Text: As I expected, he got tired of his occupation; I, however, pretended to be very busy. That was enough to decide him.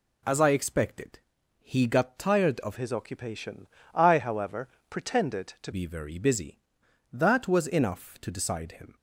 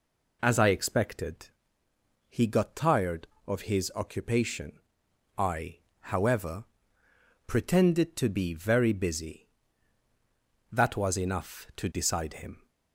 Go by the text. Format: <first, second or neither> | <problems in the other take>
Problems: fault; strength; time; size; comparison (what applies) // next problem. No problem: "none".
second | changes voice from "his" to "to"; from 2.7 to 5.7 s; 3.0 s long